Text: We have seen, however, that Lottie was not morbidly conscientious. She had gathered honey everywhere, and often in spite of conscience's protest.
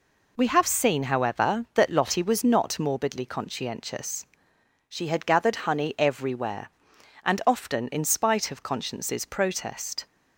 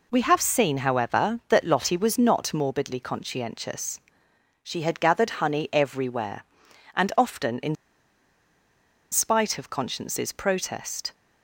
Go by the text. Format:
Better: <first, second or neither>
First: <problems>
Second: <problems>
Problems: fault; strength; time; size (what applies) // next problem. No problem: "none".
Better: first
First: none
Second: pauses between "in" and "spite"; strong; at 7.7 s; 1.3 s long